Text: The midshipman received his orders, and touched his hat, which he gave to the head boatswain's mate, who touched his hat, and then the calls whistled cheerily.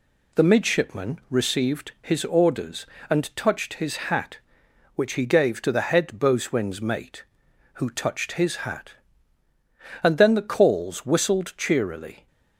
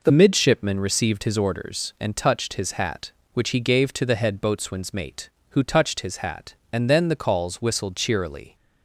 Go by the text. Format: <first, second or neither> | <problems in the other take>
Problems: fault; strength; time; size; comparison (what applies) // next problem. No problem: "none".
first | changes voice at "midshipman"; from 0.0 s on; 8.5 s long